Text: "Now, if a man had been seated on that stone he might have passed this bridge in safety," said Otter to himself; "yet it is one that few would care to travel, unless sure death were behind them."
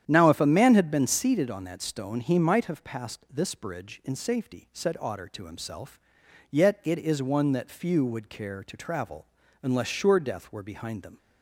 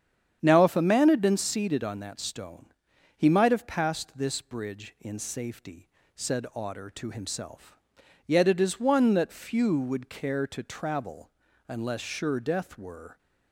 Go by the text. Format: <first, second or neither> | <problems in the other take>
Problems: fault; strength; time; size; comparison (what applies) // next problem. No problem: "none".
first | starts louder than the rest; strong; until 1.4 s; 8.5 dB; strong in the first // pauses between "stone" and "he"; noticeable; at 2.7 s; 0.46 s long // stops before "behind them"; at 13.1 s